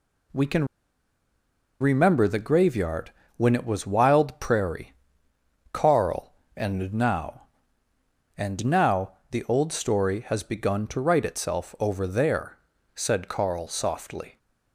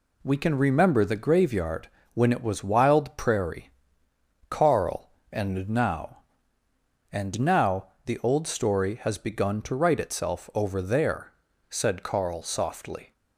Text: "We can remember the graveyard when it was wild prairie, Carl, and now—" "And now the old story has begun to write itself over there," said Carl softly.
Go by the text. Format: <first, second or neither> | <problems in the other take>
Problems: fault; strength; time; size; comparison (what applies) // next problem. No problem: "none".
second | pauses between "can" and "remember"; at 0.6 s; 1.1 s long // pauses between "graveyard" and "when"; slight; at 3.1 s; 0.24 s long; slight in the second // pauses between "now" and "the"; slight; at 9.1 s; 0.18 s long; slight in the second